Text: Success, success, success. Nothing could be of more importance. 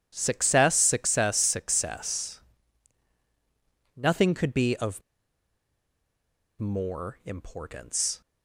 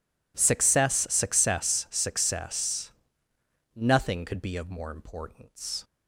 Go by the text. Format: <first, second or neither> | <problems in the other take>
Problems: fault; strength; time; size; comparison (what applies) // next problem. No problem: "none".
second | pauses between "of" and "more"; strong; at 5.0 s; 1.5 s long